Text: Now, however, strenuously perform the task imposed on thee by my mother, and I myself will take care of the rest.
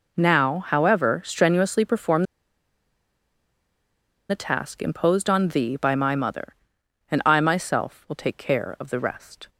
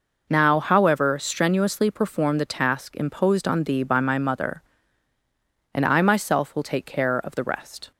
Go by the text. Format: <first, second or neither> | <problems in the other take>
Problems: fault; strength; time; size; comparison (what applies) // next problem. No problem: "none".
second | pauses between "perform" and "the"; strong; at 2.2 s; 2.0 s long